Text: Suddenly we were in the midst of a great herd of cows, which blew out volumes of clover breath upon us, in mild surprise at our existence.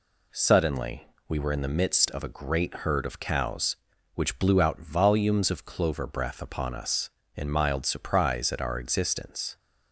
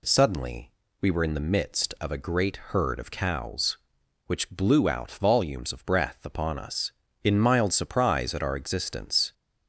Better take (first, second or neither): first